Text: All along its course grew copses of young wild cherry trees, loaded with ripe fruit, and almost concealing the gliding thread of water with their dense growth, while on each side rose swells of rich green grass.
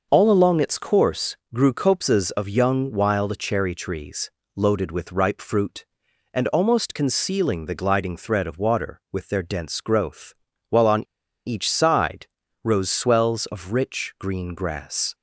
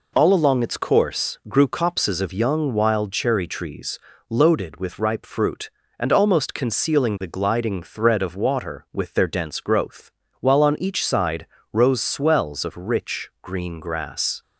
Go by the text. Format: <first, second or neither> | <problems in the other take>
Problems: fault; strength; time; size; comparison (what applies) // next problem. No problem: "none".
second | starts louder than the rest; noticeable; until 1.1 s; 6 dB // pauses between "course" and "grew"; slight; at 1.3 s; 0.16 s long // pauses between "on" and "each"; at 11.0 s; 0.43 s long // pauses between "side" and "rose"; at 12.2 s; 0.40 s long; slight in the second